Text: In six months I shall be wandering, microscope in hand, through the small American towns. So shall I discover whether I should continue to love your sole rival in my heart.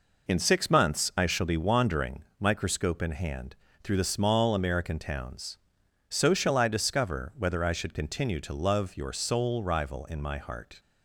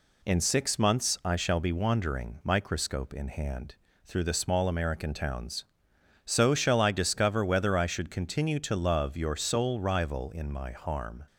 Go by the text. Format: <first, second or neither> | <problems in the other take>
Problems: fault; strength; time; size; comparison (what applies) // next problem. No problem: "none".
first | says "harm" for "heart"; at 10.7 s